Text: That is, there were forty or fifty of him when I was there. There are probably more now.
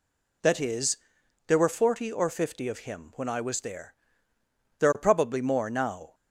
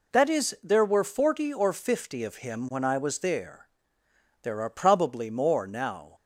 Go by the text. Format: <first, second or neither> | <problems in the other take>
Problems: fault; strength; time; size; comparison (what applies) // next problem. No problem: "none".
neither | none